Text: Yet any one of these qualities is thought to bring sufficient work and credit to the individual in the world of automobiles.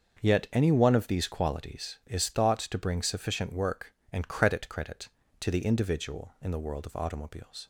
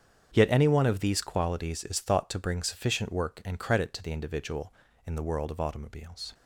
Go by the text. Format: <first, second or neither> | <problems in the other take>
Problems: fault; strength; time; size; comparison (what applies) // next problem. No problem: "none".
second | starts louder than the rest; until 1.2 s; 7 dB; strong in the second // says "credit" twice; at 4.6 s